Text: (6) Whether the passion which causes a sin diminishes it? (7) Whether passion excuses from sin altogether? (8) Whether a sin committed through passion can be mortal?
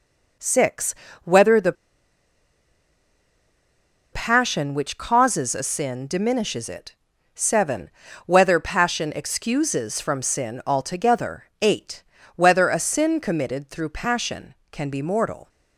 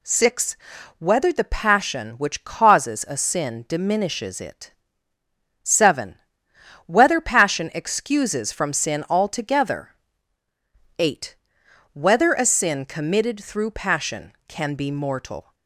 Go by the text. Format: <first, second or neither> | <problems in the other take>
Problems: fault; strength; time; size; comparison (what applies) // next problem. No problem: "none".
second | pauses between "the" and "passion"; strong; at 1.7 s; 2.3 s long